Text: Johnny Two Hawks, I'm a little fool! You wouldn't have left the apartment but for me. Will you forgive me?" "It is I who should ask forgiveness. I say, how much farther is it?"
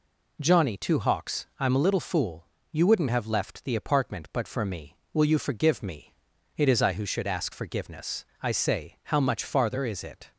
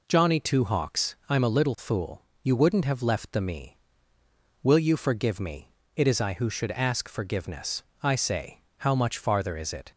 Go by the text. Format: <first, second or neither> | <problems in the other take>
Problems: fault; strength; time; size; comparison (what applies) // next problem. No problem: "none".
first | skips "apartment but for"; at 3.4 s